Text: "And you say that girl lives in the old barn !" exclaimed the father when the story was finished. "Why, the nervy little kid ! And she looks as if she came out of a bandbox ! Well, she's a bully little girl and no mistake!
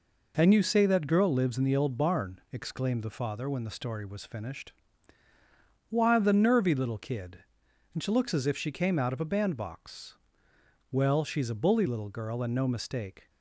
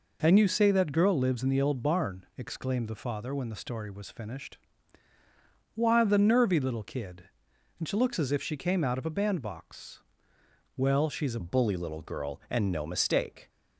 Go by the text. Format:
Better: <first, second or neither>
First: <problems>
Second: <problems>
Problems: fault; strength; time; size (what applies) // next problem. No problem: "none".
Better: first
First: none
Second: changes voice at "bully"; from 11.4 s on; 2.0 s long